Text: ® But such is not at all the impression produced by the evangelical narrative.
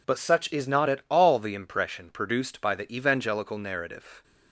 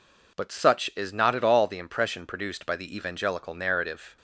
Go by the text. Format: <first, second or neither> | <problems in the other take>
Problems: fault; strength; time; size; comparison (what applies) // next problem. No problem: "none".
neither | none